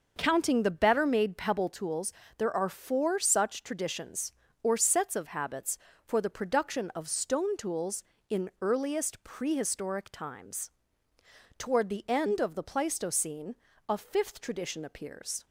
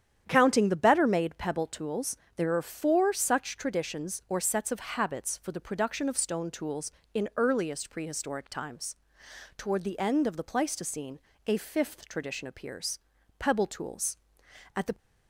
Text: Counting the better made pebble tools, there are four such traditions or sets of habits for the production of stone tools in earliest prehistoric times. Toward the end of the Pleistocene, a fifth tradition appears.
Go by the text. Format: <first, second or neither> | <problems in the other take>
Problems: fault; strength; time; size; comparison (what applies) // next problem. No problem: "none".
first | starts louder than the rest; strong; until 1.2 s; 9.5 dB; noticeable in the first // goes on to say "PEBBLE TOOLS At the"; from 13.3 s on; 1.5 s long